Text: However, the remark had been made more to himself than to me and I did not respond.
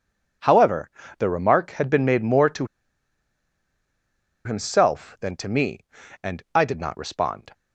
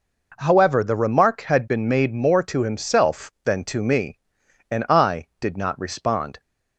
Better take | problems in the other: second | pauses between "to" and "himself"; strong; at 2.6 s; 1.7 s long

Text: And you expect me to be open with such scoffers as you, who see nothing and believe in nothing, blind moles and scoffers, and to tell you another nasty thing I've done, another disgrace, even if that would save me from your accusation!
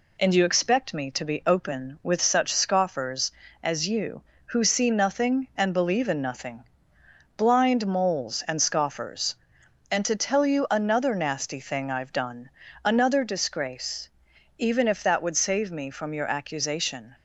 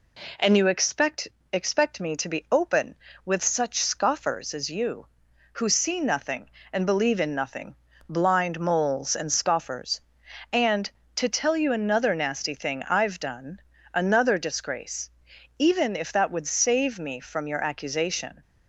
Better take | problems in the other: first | says "expect" twice; at 1.5 s

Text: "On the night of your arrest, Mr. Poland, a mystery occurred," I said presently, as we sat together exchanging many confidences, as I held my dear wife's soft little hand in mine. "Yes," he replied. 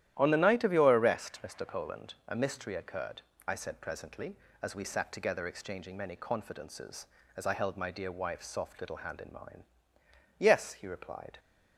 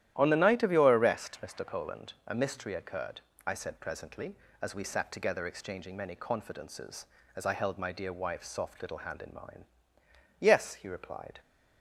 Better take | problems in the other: neither | starts louder than the rest; strong; the same in both

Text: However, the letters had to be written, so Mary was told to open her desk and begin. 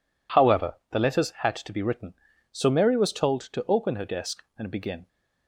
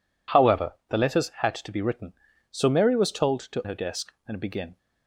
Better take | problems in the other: first | skips "open"; at 3.6 s

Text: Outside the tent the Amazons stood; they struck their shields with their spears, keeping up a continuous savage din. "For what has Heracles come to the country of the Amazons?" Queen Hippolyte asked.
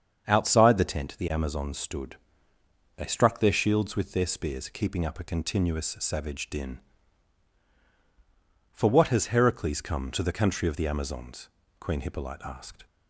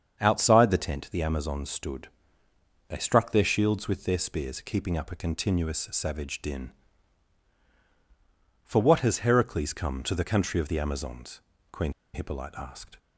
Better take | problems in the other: first | starts louder than the rest; strong; until 1.2 s; 7 dB; strong in the first // pauses between "Queen" and "Hippolyte"; slight; at 11.9 s; 0.22 s long

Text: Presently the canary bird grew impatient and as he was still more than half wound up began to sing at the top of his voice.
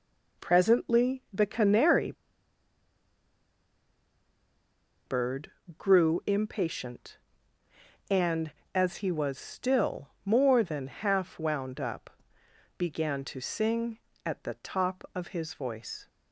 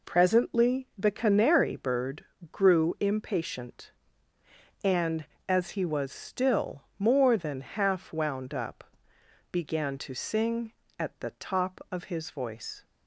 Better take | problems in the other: second | pauses between "canary" and "bird"; strong; at 2.1 s; 2.9 s long // pauses between "bird" and "grew"; slight; at 5.5 s; 0.26 s long; slight in the second // pauses between "still" and "more"; slight; at 10.0 s; 0.16 s long; slight in the second // pauses between "up" and "began"; noticeable; at 12.0 s; 0.68 s long; noticeable in the second

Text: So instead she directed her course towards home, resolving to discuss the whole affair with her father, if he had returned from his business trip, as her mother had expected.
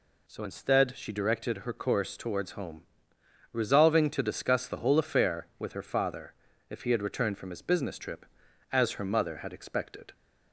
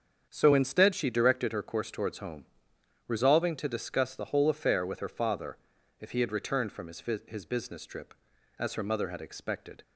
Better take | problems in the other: first | starts louder than the rest; strong; until 1.3 s; 7.5 dB // says "his" twice; at 7.2 s

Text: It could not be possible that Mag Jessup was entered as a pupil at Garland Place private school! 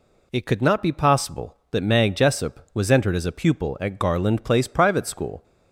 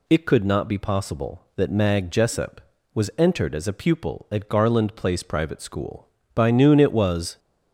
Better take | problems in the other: first | goes on to say "By noon it was"; noticeable; from 6.3 s on; 1.0 s long

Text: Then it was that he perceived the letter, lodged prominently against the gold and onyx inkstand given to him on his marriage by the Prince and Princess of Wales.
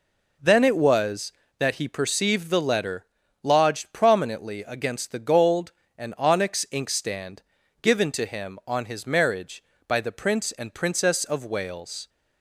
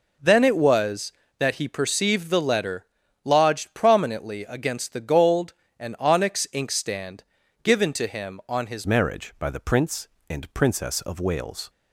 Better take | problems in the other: first | pauses between "inkstand" and "given"; at 7.2 s; 0.38 s long; also in the first // changes voice at "marriage"; from 8.8 s on; 2.8 s long

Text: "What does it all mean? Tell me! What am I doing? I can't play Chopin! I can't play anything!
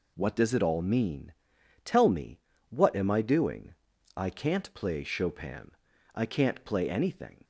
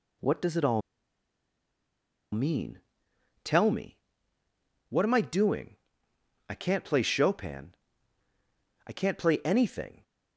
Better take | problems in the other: first | pauses between "all" and "mean"; strong; at 0.8 s; 1.5 s long

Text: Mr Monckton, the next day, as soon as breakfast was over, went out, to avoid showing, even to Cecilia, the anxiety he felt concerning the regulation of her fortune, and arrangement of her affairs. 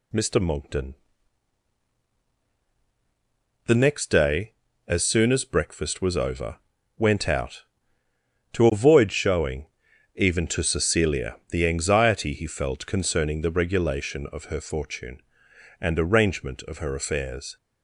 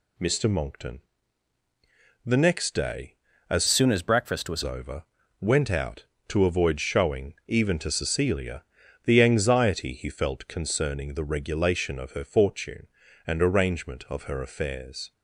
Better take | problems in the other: first | changes voice from "soon" to "was"; from 3.6 to 4.6 s; 1.0 s long

